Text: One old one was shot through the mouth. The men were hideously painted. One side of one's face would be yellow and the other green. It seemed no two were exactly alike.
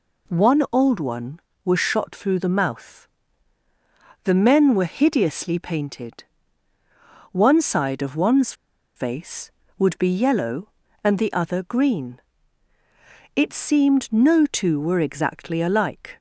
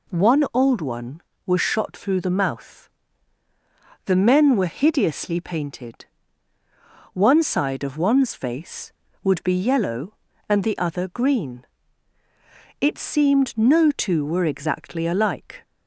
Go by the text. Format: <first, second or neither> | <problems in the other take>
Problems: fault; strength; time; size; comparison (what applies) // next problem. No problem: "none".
second | pauses between "one's" and "face"; at 8.5 s; 0.43 s long